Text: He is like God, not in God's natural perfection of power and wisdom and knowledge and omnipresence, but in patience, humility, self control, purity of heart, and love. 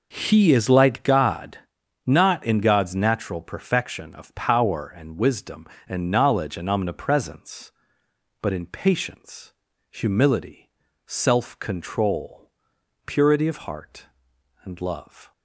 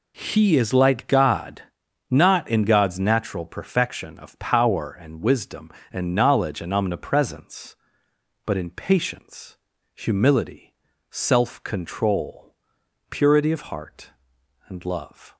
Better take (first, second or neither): second